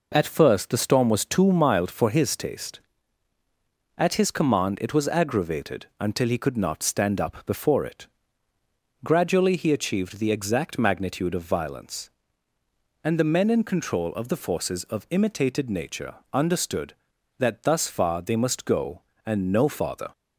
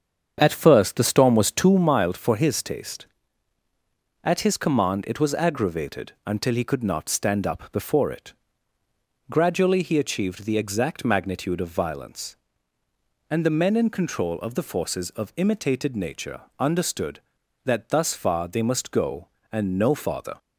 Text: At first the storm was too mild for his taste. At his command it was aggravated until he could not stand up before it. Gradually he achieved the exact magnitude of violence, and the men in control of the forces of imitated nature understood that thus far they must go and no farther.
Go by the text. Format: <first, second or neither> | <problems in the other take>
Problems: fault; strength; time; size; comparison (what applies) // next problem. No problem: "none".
first | starts louder than the rest; strong; until 1.8 s; 7.5 dB // pauses between "nature" and "understood"; slight; at 16.4 s; 0.16 s long; slight in the first